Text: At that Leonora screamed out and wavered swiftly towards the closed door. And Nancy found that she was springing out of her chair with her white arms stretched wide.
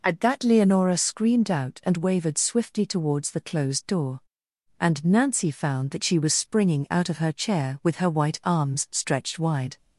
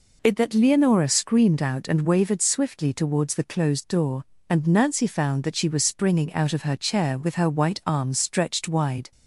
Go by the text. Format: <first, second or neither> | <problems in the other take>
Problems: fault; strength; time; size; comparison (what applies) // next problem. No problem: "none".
first | says "It" for "At"; at 0.2 s